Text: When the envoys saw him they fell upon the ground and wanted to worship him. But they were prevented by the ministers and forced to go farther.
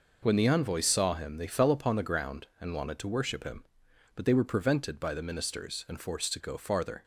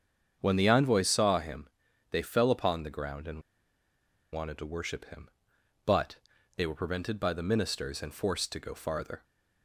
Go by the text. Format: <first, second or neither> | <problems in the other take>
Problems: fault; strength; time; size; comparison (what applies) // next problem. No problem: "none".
first | starts louder than the rest; strong; until 1.4 s; 7.5 dB // pauses between "him" and "they"; at 1.6 s; 0.44 s long // pauses between "and" and "wanted"; noticeable; at 3.4 s; 0.91 s long // pauses between "But" and "they"; at 6.1 s; 0.40 s long